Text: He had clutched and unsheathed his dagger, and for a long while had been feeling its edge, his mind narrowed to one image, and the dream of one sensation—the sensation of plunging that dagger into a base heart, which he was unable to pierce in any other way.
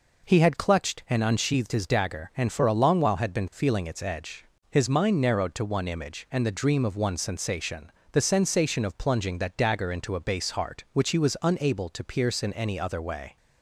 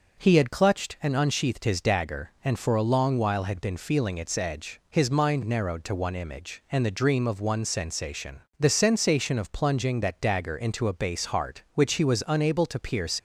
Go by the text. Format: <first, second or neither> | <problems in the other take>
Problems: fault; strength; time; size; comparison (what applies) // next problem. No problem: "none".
first | stops before "in any other way"; at 13.1 s